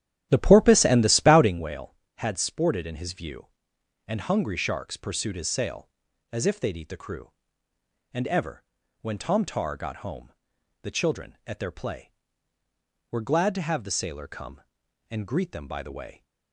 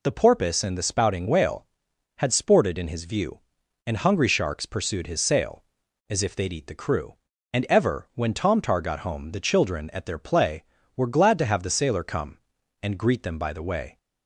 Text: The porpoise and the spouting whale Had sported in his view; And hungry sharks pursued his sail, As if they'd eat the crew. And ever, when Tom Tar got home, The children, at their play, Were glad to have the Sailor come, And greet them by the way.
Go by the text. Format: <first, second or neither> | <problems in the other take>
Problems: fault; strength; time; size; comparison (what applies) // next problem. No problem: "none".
second | starts louder than the rest; strong; until 1.6 s; 11.5 dB